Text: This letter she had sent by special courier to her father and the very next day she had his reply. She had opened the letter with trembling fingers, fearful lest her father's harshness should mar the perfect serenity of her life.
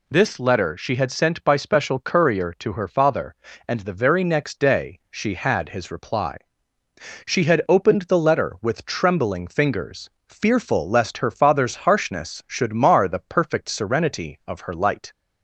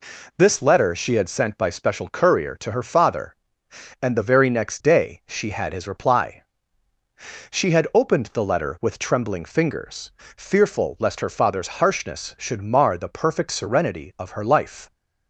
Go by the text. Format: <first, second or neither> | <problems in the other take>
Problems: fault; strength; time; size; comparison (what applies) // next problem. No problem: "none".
second | says "light" for "life"; at 14.7 s